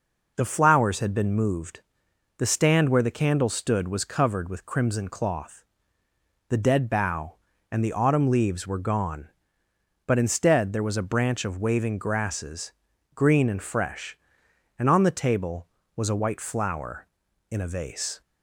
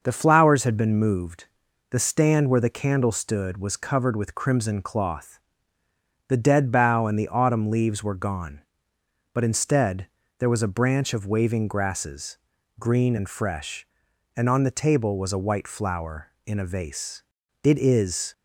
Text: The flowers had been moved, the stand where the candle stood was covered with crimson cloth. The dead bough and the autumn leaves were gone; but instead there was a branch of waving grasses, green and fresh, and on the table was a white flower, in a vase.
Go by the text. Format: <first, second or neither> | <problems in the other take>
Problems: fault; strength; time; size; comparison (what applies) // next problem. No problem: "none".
first | starts louder than the rest; noticeable; until 1.0 s; 6 dB // pauses between "instead" and "there"; slight; at 10.0 s; 0.32 s long // goes on to say "It is"; noticeable; from 17.6 s on; 0.70 s long